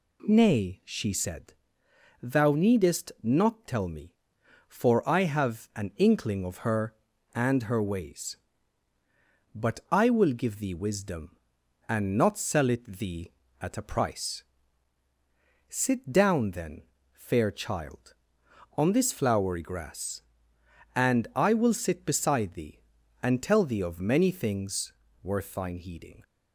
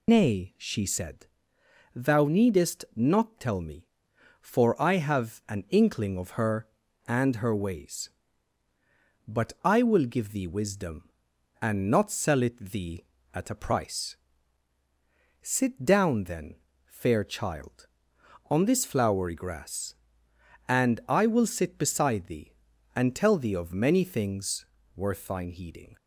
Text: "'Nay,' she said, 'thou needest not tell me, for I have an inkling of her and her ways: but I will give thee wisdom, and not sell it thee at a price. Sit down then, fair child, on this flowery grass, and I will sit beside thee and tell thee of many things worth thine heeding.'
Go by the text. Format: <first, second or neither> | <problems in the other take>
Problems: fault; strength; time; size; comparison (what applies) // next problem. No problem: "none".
first | loses the start of "Nay"; at 0.0 s; 155 ms // pauses between "things" and "worth"; slight; at 24.6 s; 0.30 s long; slight in the first